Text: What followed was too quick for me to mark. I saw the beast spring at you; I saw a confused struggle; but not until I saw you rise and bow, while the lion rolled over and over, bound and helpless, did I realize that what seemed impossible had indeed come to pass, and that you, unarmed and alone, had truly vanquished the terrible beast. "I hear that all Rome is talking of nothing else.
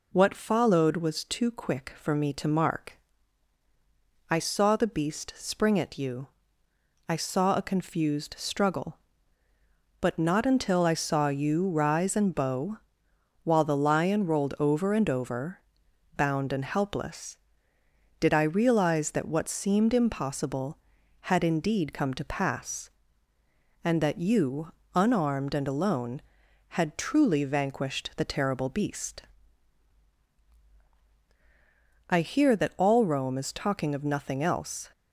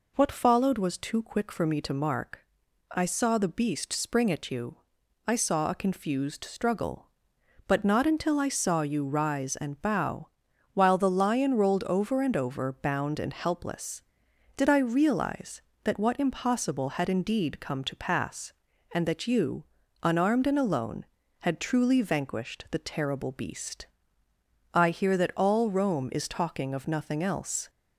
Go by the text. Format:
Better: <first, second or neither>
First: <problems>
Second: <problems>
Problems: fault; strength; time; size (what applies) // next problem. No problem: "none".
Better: first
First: none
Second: skips "seemed"; at 16.1 s